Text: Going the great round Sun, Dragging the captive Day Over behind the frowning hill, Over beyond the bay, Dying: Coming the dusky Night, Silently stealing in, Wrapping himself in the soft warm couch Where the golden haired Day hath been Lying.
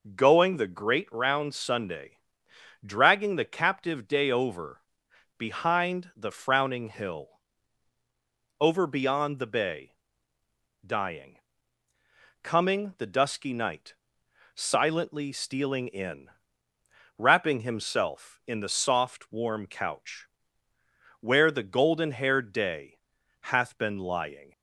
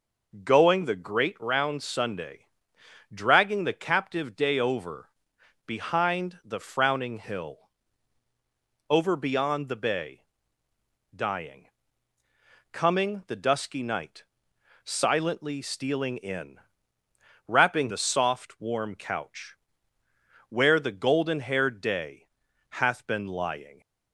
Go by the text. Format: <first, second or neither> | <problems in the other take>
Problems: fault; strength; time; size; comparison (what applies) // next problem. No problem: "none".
first | pauses between "Over" and "behind"; noticeable; at 5.0 s; 0.56 s long; noticeable in the first // skips "himself in"; at 17.8 s // pauses between "couch" and "Where"; noticeable; at 19.5 s; 0.92 s long; noticeable in the first // pauses between "Day" and "hath"; at 22.2 s; 0.42 s long; also in the first